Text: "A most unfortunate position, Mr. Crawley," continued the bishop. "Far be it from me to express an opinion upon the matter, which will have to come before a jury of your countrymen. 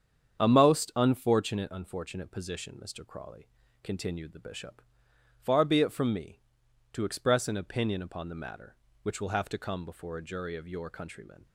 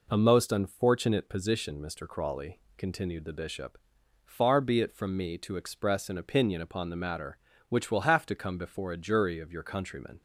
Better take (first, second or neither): second